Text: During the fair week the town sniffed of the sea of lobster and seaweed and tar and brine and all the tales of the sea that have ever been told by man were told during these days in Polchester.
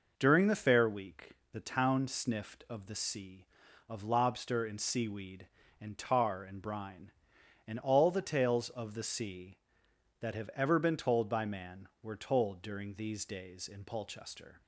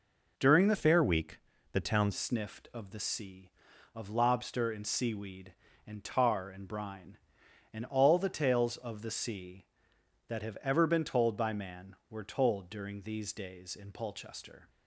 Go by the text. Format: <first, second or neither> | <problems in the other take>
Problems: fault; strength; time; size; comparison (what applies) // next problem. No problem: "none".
first | changes voice from "fair" to "town"; from 0.7 to 2.1 s; 1.4 s long // pauses between "week" and "the"; slight; at 1.3 s; 0.34 s long; slight in the first